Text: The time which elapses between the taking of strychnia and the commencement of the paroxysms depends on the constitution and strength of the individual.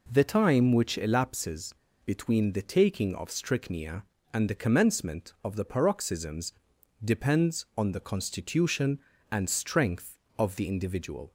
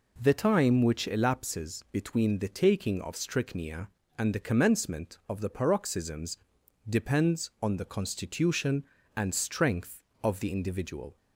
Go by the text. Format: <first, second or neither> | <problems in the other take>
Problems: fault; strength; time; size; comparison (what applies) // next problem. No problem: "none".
second | pauses between "elapses" and "between"; slight; at 1.7 s; 0.29 s long // pauses between "paroxysms" and "depends"; noticeable; at 6.5 s; 0.50 s long; noticeable in the second